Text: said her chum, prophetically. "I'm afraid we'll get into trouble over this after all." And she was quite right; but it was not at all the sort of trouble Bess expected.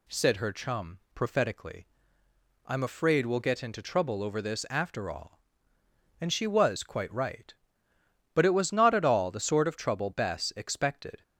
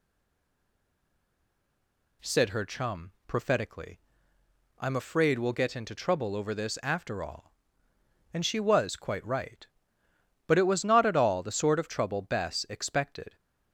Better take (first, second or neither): first